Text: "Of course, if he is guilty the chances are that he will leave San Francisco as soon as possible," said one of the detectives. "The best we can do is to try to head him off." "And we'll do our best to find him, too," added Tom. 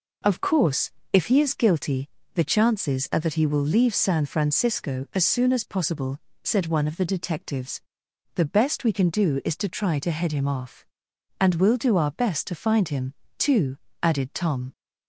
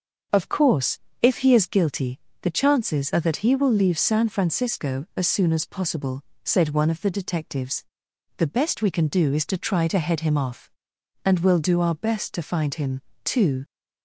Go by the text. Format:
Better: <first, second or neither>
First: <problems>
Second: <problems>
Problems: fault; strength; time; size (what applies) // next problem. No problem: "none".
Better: first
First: pauses between "guilty" and "the"; slight; at 2.0 s; 0.26 s long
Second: starts louder than the rest; until 1.5 s; 7 dB // pauses between "guilty" and "the"; slight; at 2.1 s; 0.22 s long // stops before "added Tom"; at 13.6 s